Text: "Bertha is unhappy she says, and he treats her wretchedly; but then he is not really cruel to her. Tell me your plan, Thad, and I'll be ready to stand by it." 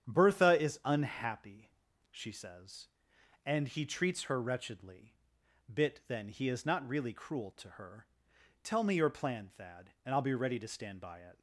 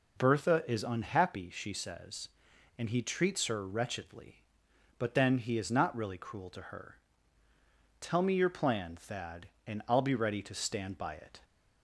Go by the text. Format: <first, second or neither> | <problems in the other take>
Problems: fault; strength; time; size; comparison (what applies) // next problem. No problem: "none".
second | starts louder than the rest; strong; until 1.1 s; 8.5 dB // pauses between "unhappy" and "she"; at 1.6 s; 0.44 s long // says "bit" for "but"; at 5.7 s